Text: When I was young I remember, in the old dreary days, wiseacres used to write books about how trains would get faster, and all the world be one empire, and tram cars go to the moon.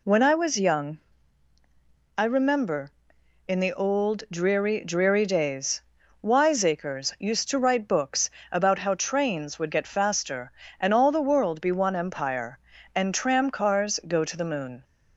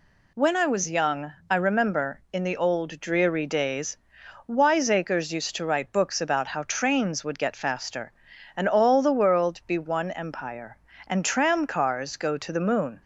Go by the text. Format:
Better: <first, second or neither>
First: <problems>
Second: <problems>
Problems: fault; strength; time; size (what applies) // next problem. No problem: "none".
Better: second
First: pauses between "young" and "I"; at 0.9 s; 1.1 s long // says "dreary" twice; at 4.8 s // pauses between "books" and "about"; slight; at 8.2 s; 0.22 s long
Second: pauses between "young" and "I"; slight; at 1.3 s; 0.16 s long